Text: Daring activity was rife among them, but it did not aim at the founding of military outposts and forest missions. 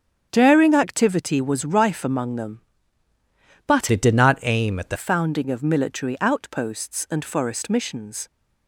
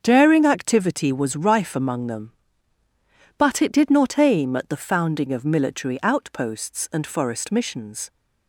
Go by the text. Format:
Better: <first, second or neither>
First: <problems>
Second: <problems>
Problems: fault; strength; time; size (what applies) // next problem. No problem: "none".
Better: second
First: starts louder than the rest; strong; until 1.3 s; 8 dB // changes voice from "it" to "the"; from 3.9 to 4.9 s; 1.0 s long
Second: starts louder than the rest; until 1.0 s; 7 dB